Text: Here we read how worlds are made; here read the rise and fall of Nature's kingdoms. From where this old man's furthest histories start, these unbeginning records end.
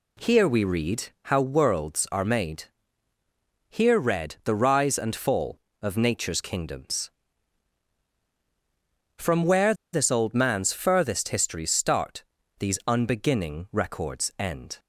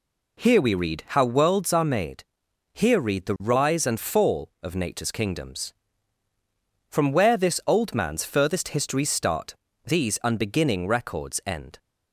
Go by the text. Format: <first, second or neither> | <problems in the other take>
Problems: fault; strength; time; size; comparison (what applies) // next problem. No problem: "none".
second | pauses between "read" and "how"; slight; at 1.0 s; 0.20 s long // pauses between "where" and "this"; slight; at 9.7 s; 0.19 s long